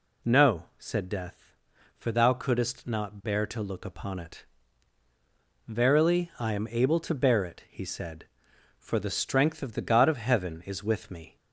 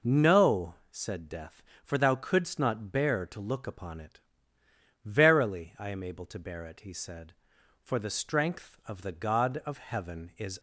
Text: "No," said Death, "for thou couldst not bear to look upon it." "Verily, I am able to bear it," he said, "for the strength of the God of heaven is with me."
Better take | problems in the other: first | stops before "with me"; at 10.5 s

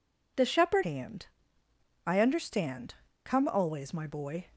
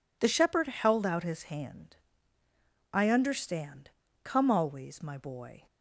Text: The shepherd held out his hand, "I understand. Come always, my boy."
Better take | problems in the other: second | skips "held out his"; at 0.8 s

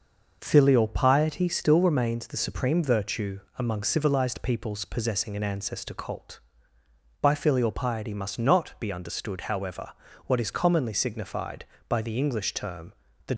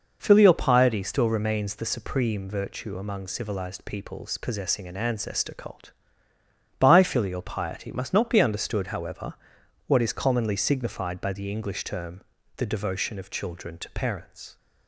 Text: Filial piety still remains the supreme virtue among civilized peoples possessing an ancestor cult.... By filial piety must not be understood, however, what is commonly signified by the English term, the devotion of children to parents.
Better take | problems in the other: second | pauses between "virtue" and "among"; slight; at 3.3 s; 0.18 s long // stops before "devotion of children to parents"; at 13.3 s

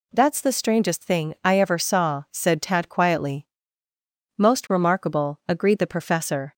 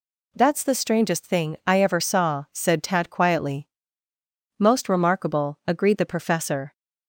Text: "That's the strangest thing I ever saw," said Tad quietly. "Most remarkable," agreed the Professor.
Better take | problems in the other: neither | none

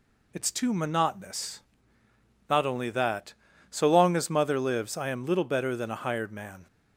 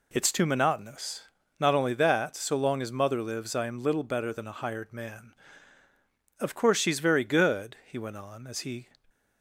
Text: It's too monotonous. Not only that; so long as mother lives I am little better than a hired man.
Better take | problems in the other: first | goes on to say "Of course she's very good he went on as he"; strong; from 6.3 s on; 2.5 s long

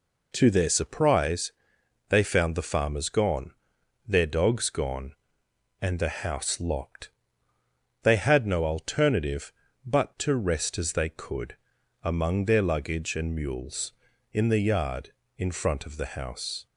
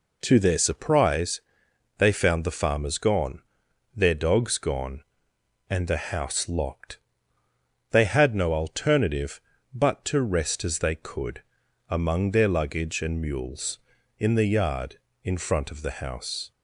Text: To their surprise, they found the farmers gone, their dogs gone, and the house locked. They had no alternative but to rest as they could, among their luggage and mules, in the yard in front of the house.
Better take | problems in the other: neither | none

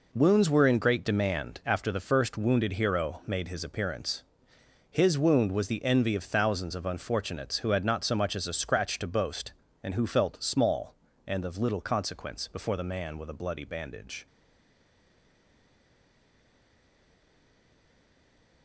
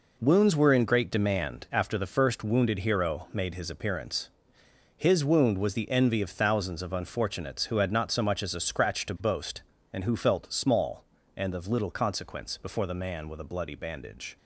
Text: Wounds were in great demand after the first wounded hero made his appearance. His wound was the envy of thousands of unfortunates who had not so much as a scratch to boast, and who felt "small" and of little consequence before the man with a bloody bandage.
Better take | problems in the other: second | stays silent after the last word; strong; from 14.2 s on; 4.4 s long

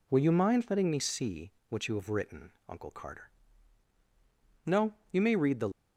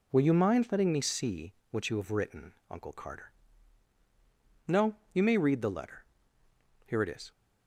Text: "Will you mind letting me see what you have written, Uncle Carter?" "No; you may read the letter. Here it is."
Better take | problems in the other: second | pauses between "see" and "what"; slight; at 1.5 s; 0.18 s long; slight in the second // stops before "letter Here it is"; at 5.7 s

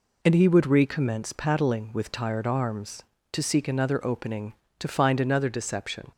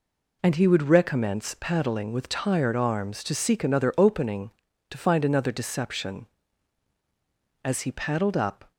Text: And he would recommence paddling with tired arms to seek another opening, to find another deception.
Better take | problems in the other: first | goes on to say "As he paddled up"; noticeable; from 7.6 s on; 1.0 s long

